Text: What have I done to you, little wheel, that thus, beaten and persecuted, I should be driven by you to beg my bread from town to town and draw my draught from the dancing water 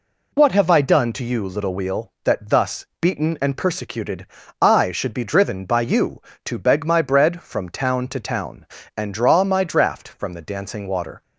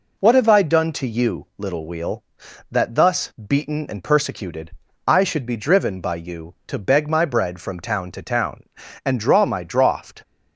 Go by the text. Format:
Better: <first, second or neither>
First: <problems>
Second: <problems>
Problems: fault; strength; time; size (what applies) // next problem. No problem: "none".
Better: first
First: none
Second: stops before "from the dancing water"; at 10.2 s